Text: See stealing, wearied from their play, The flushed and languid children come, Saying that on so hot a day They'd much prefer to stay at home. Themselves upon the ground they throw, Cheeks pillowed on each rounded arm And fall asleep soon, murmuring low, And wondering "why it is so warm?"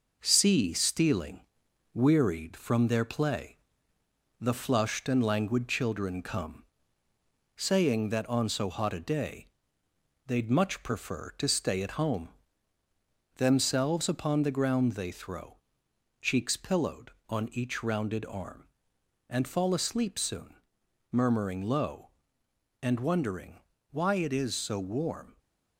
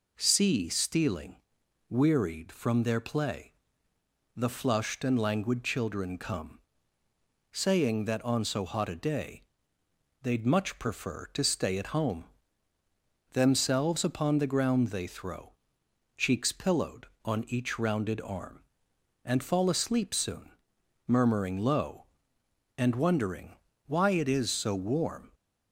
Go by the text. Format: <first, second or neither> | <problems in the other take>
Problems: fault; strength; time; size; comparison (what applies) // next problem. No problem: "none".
second | gets quieter; noticeable; throughout; 4 dB // pauses between "day" and "They'd"; noticeable; at 9.4 s; 0.80 s long; noticeable in the second // pauses between "wondering" and "why"; slight; at 23.6 s; 0.30 s long; slight in the second